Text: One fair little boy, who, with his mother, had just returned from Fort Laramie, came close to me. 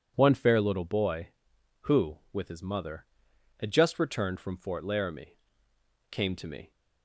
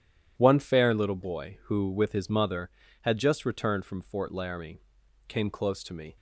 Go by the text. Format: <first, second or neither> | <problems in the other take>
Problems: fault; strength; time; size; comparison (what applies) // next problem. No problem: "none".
second | skips "close"; at 6.3 s